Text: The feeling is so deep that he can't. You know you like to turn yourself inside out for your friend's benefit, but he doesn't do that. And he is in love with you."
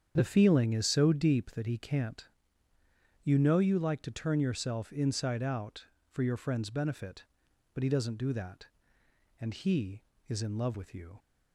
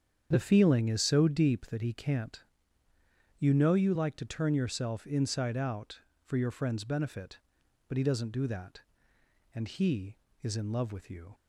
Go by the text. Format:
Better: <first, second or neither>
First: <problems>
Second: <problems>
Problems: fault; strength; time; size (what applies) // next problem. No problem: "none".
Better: neither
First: starts louder than the rest; strong; until 1.1 s; 8 dB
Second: starts louder than the rest; strong; until 1.3 s; 8 dB